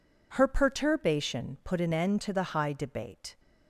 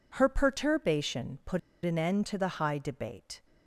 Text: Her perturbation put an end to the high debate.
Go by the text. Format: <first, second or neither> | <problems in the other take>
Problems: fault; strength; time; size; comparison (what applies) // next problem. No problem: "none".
first | pauses between "put" and "an"; slight; at 1.5 s; 0.26 s long